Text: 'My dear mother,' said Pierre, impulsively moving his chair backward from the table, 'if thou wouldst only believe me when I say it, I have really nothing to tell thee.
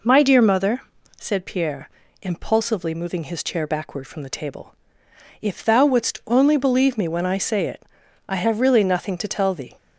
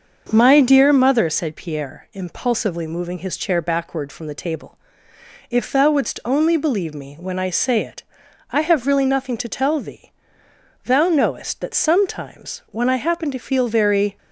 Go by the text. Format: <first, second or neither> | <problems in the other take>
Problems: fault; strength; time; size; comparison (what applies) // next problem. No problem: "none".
first | starts louder than the rest; until 1.3 s; 6.5 dB // goes on to say "Thou knowest that sometimes when I happen to feel very"; strong; from 10.8 s on; 3.3 s long